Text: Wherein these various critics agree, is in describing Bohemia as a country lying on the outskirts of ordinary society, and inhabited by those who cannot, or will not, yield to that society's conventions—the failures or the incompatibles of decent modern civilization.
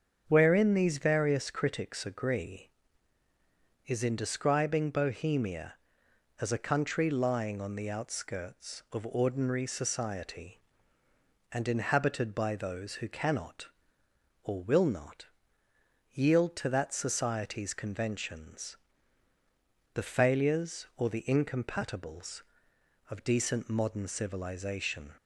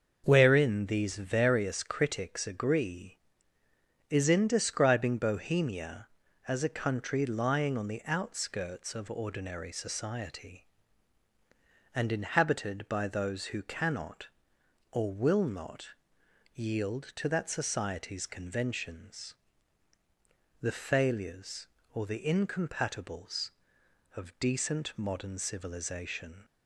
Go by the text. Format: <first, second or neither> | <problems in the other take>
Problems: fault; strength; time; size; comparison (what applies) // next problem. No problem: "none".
neither | starts louder than the rest; the same in both